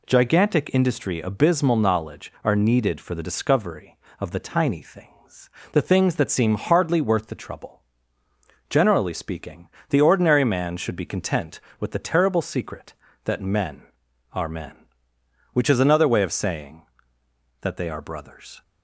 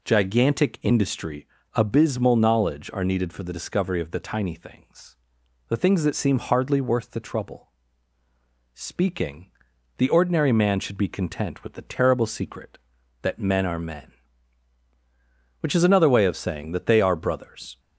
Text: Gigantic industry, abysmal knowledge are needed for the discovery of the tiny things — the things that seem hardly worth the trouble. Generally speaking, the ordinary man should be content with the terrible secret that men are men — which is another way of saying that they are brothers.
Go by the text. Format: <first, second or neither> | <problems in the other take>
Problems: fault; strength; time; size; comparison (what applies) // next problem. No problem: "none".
first | skips "Generally"; at 8.2 s